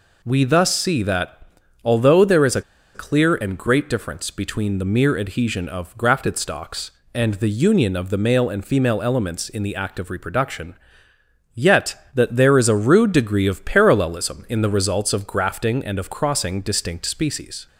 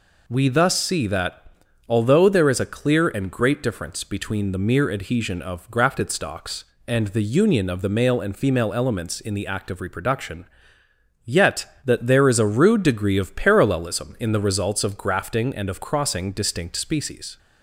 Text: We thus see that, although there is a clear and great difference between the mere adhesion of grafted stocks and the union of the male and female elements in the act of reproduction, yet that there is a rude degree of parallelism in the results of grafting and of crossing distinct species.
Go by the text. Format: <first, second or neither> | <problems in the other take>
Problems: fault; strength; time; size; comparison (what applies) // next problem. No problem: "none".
second | pauses between "a" and "clear"; slight; at 2.6 s; 0.32 s long